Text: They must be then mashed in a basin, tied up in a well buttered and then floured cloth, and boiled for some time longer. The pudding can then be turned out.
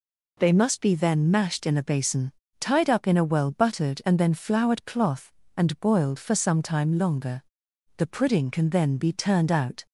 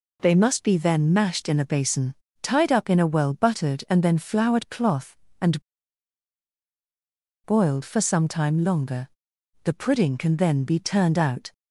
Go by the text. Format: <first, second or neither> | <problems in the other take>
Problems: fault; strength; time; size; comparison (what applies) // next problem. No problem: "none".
first | pauses between "and" and "boiled"; strong; at 5.6 s; 1.8 s long